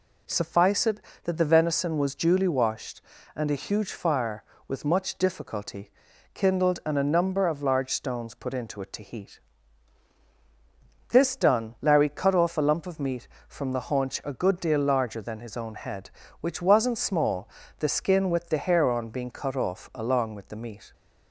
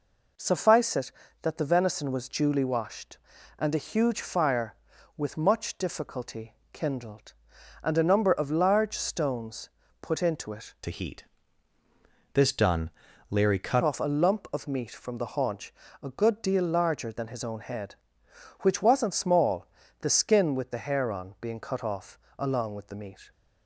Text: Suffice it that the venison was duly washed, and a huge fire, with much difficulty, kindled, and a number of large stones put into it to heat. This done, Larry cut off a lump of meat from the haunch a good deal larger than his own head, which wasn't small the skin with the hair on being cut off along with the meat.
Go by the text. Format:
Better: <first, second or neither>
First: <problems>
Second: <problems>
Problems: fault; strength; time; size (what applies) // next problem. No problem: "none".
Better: first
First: pauses between "small" and "the"; slight; at 17.4 s; 0.30 s long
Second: pauses between "stones" and "put"; slight; at 9.6 s; 0.32 s long // changes voice from "to" to "cut"; from 10.8 to 13.8 s; 3.0 s long // pauses between "haunch" and "a"; slight; at 15.7 s; 0.28 s long // pauses between "small" and "the"; slight; at 19.6 s; 0.36 s long // pauses between "off" and "along"; slight; at 22.1 s; 0.20 s long